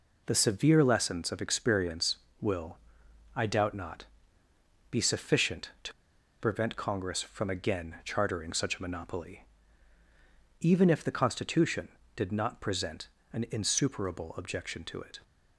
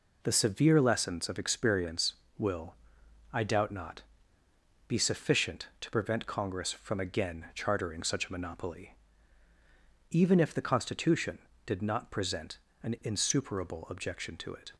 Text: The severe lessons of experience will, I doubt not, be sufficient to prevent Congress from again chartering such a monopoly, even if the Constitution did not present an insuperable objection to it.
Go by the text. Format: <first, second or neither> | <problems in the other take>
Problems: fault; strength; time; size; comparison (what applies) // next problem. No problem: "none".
second | pauses between "to" and "prevent"; noticeable; at 5.9 s; 0.48 s long // pauses between "present" and "an"; slight; at 13.0 s; 0.24 s long; slight in the second